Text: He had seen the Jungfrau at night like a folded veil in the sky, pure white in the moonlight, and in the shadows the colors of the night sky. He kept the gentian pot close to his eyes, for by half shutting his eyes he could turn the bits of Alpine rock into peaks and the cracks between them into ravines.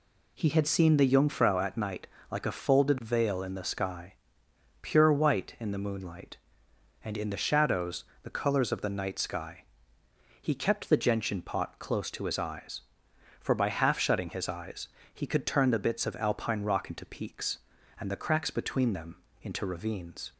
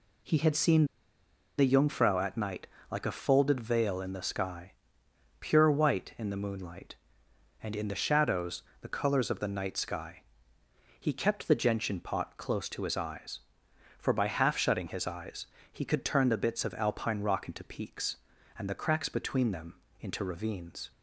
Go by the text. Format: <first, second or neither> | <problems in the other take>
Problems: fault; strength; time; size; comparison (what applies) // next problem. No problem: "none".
first | pauses between "seen" and "the"; noticeable; at 0.8 s; 0.72 s long // pauses between "night" and "like"; slight; at 2.6 s; 0.22 s long; slight in the first // pauses between "shadows" and "the"; slight; at 8.6 s; 0.16 s long; slight in the first // pauses between "eyes" and "he"; slight; at 15.4 s; 0.24 s long; slight in the first // pauses between "them" and "into"; slight; at 19.7 s; 0.24 s long; slight in the first